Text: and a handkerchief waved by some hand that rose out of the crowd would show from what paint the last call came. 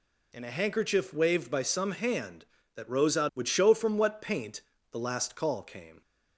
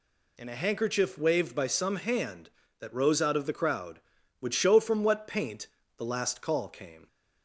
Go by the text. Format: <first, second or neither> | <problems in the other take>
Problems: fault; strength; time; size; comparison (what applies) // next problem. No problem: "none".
second | skips "of the crowd"; at 3.3 s // pauses between "paint" and "the"; slight; at 4.6 s; 0.30 s long; slight in the second